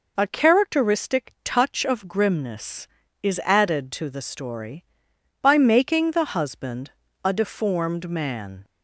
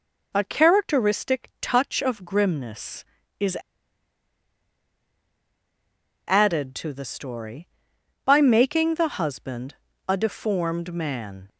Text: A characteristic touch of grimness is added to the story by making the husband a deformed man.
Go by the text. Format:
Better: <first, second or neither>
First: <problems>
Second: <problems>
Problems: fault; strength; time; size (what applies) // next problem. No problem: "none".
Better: first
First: pauses between "husband" and "a"; slight; at 6.9 s; 0.32 s long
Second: pauses between "is" and "added"; strong; at 3.5 s; 2.7 s long // pauses between "husband" and "a"; slight; at 9.7 s; 0.32 s long